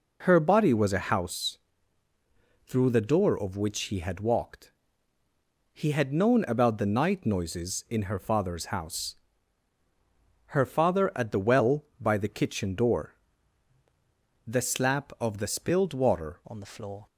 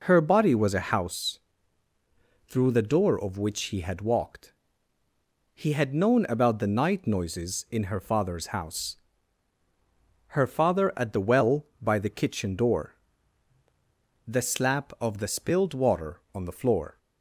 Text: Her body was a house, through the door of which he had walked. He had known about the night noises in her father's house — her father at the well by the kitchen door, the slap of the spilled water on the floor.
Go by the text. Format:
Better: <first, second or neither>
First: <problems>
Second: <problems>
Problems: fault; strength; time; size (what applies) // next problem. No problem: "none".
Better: second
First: changes voice at "on"; from 16.4 s on; 0.6 s long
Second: none